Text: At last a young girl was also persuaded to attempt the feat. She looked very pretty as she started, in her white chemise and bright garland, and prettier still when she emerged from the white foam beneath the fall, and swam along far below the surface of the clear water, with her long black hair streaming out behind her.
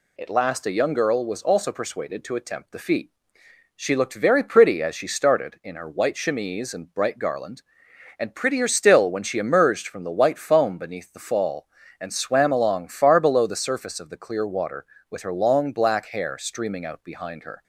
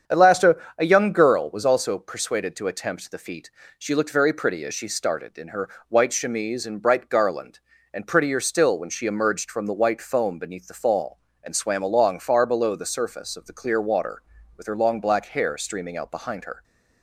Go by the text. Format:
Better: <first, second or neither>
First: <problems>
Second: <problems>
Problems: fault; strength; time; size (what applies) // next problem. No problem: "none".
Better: first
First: none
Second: starts louder than the rest; strong; until 1.2 s; 7.5 dB // says "a" twice; at 0.7 s // pauses between "her" and "white"; slight; at 5.6 s; 0.22 s long